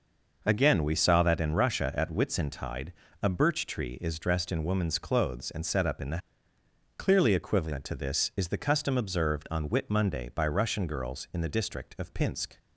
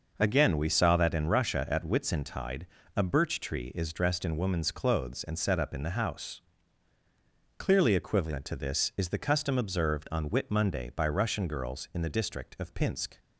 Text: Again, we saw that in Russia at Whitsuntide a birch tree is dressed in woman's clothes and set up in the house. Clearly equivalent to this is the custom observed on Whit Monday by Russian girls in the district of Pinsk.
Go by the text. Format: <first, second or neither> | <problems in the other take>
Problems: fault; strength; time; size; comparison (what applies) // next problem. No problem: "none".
second | pauses between "Whitsuntide" and "a"; slight; at 2.9 s; 0.28 s long; slight in the second // skips "house"; at 6.5 s